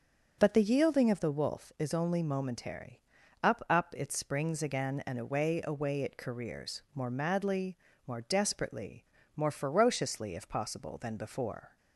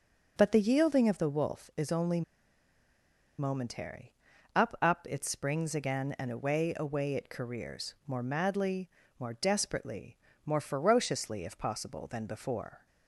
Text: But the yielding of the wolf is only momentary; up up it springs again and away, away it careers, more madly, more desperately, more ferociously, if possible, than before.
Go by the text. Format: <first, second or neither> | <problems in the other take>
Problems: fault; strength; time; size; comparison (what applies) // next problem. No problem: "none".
first | pauses between "only" and "momentary"; at 2.2 s; 1.1 s long